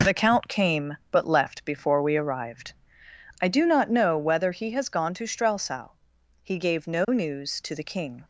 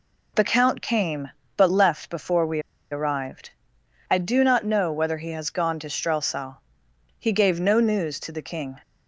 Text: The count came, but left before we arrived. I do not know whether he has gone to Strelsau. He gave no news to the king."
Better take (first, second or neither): first